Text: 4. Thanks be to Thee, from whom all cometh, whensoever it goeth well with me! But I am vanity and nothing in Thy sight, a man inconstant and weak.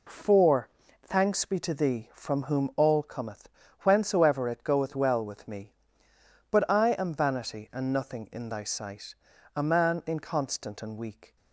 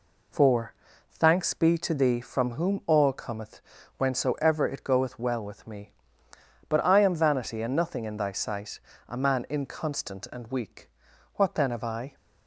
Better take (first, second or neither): first